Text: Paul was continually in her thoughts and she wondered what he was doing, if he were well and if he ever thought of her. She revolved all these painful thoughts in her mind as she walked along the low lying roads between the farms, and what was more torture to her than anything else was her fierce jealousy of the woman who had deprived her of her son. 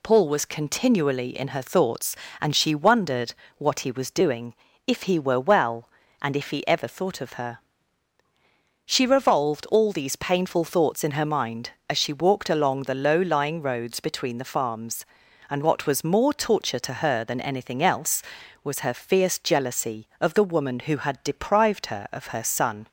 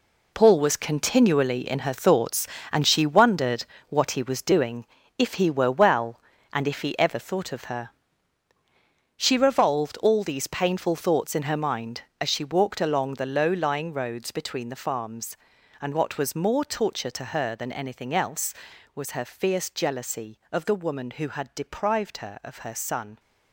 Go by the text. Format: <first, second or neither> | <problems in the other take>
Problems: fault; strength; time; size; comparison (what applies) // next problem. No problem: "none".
first | gets quieter; strong; throughout; 10 dB // pauses between "wondered" and "what"; slight; at 3.6 s; 0.24 s long; slight in the first